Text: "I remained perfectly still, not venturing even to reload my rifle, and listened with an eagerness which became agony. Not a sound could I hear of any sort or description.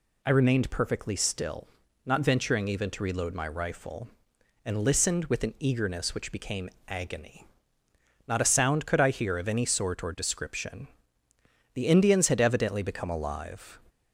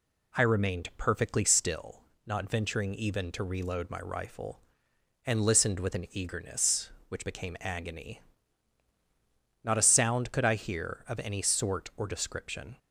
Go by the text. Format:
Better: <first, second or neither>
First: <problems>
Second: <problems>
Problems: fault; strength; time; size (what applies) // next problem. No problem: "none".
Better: second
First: pauses between "became" and "agony"; slight; at 6.6 s; 0.20 s long // goes on to say "The Indians had evidently become alive"; strong; from 11.7 s on; 2.0 s long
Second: none